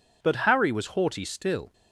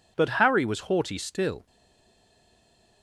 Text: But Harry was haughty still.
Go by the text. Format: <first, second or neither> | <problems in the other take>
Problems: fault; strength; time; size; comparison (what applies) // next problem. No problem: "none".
first | stays silent after the last word; noticeable; from 1.6 s on; 1.4 s long